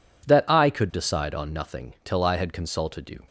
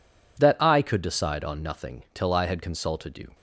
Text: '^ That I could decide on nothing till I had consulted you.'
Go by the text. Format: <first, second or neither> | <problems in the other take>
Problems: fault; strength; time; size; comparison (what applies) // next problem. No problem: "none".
neither | none